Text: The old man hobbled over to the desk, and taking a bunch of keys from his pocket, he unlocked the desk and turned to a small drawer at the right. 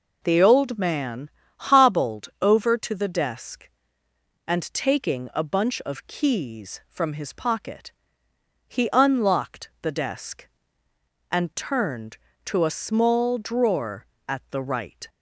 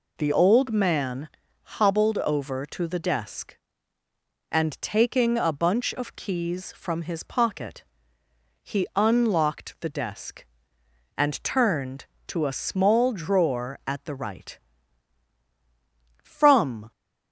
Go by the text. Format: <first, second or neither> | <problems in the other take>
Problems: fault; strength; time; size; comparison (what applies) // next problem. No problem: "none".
first | pauses between "man" and "hobbled"; slight; at 1.2 s; 0.34 s long; slight in the first // goes on to say "From"; noticeable; from 16.2 s on; 0.70 s long